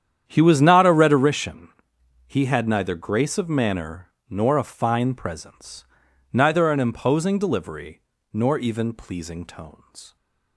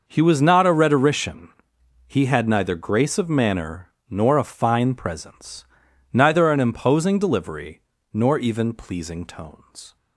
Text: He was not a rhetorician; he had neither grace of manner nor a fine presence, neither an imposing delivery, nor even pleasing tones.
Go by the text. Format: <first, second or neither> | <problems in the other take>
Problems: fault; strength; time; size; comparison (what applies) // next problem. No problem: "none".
second | starts louder than the rest; strong; until 1.4 s; 9 dB // pauses between "manner" and "nor"; slight; at 4.0 s; 0.20 s long; slight in the second